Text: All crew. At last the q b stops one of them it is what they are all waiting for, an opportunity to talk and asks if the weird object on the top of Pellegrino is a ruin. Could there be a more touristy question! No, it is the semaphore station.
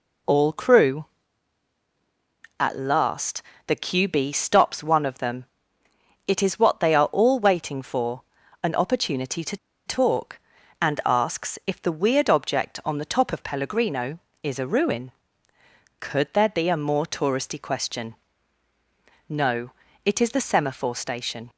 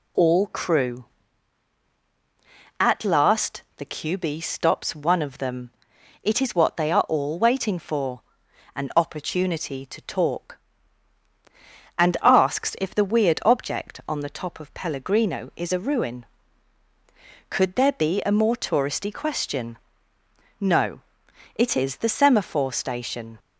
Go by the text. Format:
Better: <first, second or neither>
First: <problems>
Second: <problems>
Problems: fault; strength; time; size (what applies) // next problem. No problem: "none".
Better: second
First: pauses between "last" and "the"; slight; at 3.4 s; 0.24 s long // pauses between "them" and "it"; noticeable; at 5.4 s; 0.80 s long // pauses between "to" and "talk"; slight; at 9.5 s; 0.30 s long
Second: pauses between "last" and "the"; slight; at 3.6 s; 0.16 s long // pauses between "them" and "it"; noticeable; at 5.6 s; 0.54 s long